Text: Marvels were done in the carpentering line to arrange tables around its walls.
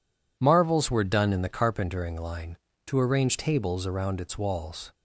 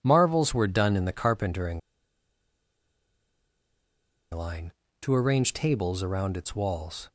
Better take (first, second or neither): first